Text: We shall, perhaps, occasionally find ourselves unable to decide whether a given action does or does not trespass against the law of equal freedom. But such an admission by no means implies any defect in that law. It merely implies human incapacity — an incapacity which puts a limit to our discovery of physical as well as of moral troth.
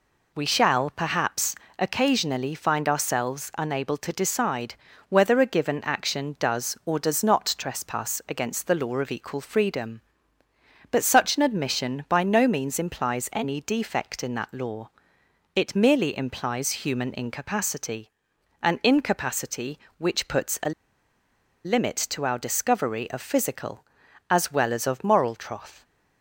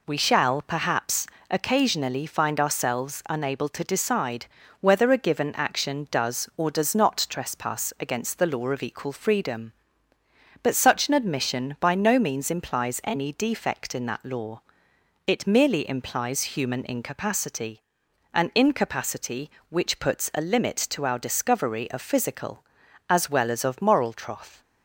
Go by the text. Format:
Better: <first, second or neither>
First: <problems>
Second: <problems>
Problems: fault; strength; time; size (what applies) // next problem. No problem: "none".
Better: second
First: pauses between "decide" and "whether"; slight; at 4.7 s; 0.34 s long // pauses between "a" and "limit"; noticeable; at 20.7 s; 0.94 s long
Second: pauses between "decide" and "whether"; slight; at 4.4 s; 0.34 s long